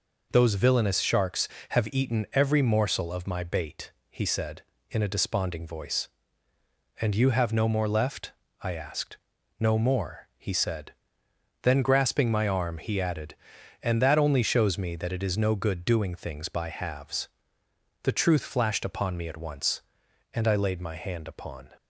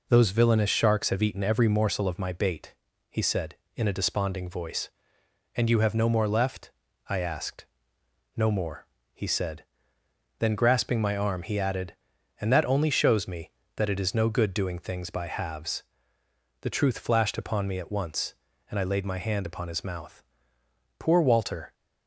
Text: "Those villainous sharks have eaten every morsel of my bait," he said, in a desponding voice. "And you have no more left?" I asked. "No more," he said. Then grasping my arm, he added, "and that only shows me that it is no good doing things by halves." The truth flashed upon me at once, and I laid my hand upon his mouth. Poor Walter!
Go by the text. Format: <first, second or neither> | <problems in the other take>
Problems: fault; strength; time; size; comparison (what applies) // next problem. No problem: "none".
second | stops before "his mouth Poor Walter"; at 21.7 s